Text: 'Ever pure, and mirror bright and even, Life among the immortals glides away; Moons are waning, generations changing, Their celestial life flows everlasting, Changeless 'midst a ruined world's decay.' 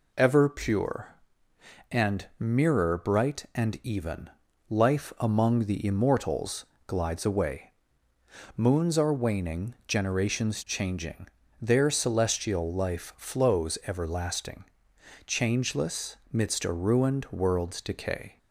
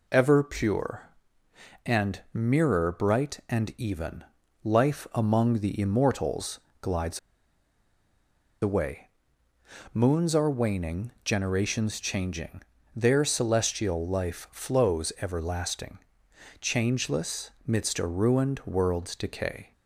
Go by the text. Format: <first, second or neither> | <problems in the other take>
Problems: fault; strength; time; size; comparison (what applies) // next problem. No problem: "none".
first | pauses between "immortals" and "glides"; slight; at 6.5 s; 0.20 s long; slight in the first // pauses between "glides" and "away"; strong; at 7.1 s; 1.4 s long // pauses between "Changeless" and "midst"; slight; at 17.4 s; 0.16 s long; slight in the first